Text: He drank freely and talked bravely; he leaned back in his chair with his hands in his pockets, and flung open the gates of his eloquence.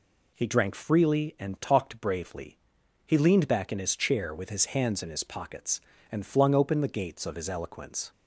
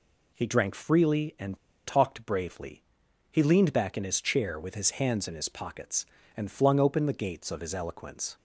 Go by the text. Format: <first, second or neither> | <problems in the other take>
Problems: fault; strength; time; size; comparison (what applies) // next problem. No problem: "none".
first | pauses between "and" and "talked"; slight; at 1.5 s; 0.28 s long